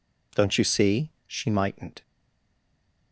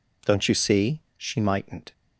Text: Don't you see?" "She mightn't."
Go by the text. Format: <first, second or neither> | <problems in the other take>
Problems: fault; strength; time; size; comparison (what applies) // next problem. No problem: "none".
second | stays silent after the last word; from 2.0 s on; 1.1 s long